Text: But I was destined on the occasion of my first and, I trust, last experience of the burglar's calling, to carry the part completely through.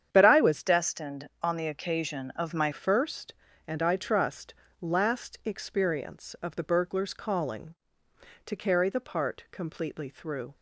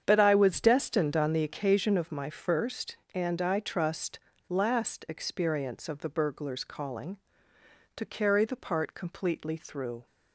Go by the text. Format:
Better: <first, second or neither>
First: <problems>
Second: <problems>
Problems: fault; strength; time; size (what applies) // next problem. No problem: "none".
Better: second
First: starts louder than the rest; strong; until 1.1 s; 8.5 dB // changes voice from "destined" to "my"; from 0.6 to 2.7 s; 2.1 s long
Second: starts louder than the rest; strong; until 1.0 s; 8 dB